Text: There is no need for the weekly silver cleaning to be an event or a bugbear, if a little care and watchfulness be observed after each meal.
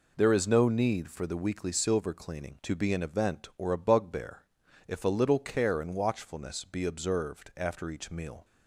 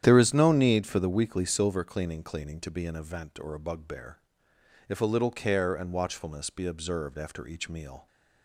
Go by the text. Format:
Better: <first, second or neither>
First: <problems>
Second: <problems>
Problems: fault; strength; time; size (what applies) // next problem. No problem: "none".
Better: first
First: none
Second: starts louder than the rest; strong; until 1.0 s; 10 dB // says "cleaning" twice; at 2.2 s